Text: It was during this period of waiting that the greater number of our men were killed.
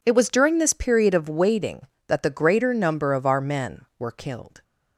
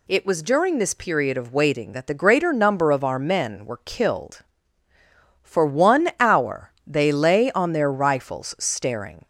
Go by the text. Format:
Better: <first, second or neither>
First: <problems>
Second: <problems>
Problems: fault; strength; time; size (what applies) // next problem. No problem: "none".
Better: first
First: none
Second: goes on to say "For one hour they lay on their rifles staring"; strong; from 5.4 s on; 3.8 s long